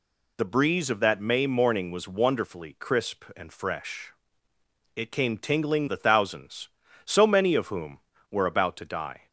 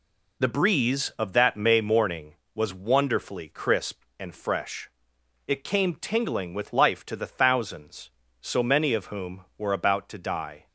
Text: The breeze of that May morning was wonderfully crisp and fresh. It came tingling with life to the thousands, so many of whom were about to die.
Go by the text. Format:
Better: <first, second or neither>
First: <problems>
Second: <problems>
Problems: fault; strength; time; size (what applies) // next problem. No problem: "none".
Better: second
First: skips "with life to"; at 5.8 s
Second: none